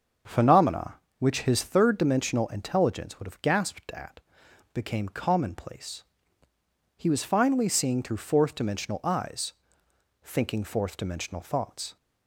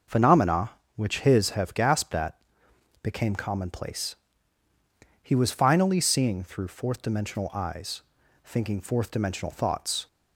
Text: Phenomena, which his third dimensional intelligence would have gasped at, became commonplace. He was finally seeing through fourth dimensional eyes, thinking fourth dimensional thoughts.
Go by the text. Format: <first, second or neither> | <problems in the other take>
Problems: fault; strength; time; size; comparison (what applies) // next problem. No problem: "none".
first | starts louder than the rest; until 1.3 s; 6 dB; also in the first // skips "third dimensional intelligence would"; at 1.5 s